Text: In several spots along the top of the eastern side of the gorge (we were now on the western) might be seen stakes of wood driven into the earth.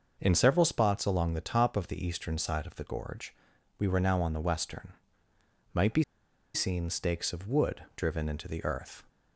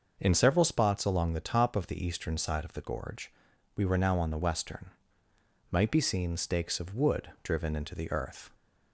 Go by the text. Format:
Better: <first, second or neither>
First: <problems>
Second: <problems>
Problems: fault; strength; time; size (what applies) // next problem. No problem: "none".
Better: second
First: starts louder than the rest; until 1.2 s; 6 dB // pauses between "be" and "seen"; noticeable; at 6.0 s; 0.50 s long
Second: starts louder than the rest; until 1.2 s; 6 dB